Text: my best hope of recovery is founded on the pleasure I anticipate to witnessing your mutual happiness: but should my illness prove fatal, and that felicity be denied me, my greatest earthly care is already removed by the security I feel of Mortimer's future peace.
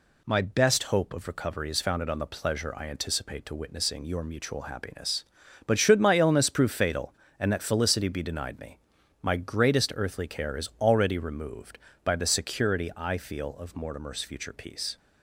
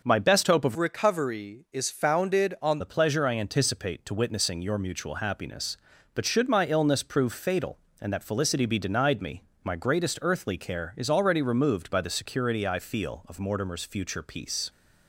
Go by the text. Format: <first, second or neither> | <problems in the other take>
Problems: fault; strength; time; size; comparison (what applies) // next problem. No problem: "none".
first | changes voice from "recovery" to "on"; from 0.7 to 2.8 s; 2.1 s long